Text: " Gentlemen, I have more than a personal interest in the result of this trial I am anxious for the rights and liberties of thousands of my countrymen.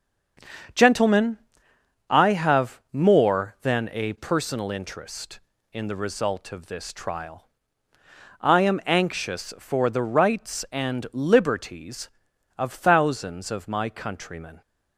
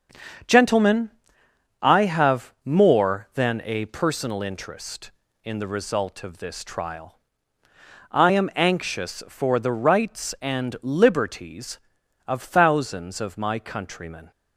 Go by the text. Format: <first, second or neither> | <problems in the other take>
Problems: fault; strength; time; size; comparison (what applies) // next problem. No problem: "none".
neither | starts louder than the rest; the same in both // pauses between "trial" and "I"; noticeable; the same in both